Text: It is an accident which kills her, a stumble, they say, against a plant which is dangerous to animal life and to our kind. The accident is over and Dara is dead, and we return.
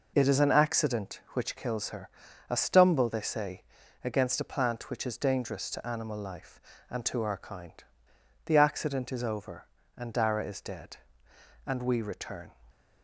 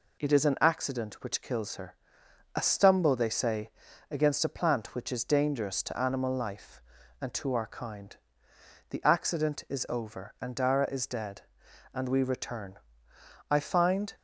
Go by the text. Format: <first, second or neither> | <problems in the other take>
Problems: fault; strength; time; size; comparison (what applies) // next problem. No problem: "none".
first | goes on to say "I find"; noticeable; from 13.4 s on; 0.64 s long